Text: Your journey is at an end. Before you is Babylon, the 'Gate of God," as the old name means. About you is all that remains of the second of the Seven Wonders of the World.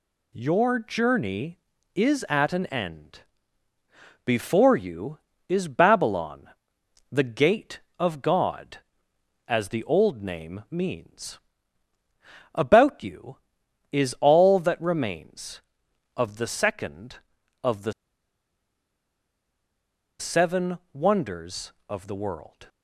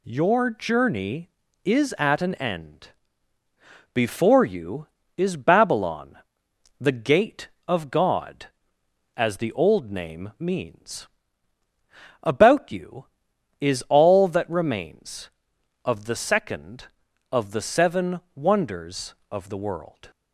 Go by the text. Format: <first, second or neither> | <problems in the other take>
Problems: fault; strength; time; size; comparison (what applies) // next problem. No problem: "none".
second | pauses between "the" and "Seven"; strong; at 17.9 s; 2.2 s long